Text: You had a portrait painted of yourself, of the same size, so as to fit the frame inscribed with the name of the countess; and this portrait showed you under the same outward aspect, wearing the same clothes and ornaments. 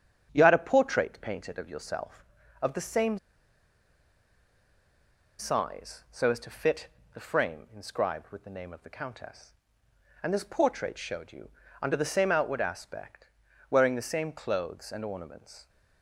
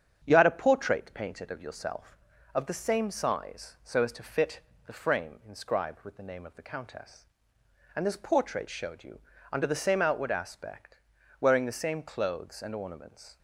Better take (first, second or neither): second